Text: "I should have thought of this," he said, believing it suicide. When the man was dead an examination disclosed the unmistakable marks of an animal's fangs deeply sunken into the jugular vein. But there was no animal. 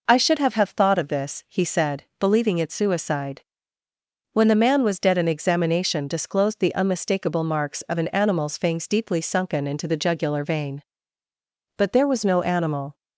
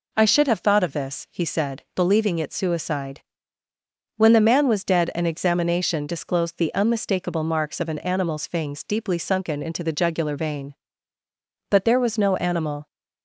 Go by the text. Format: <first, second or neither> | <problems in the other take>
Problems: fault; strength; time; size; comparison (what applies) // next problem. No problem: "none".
second | says "have" twice; at 0.5 s